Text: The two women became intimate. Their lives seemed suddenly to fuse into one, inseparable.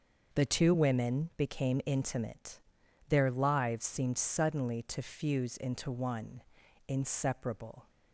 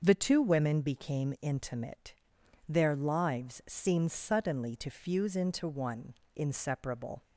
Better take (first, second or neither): neither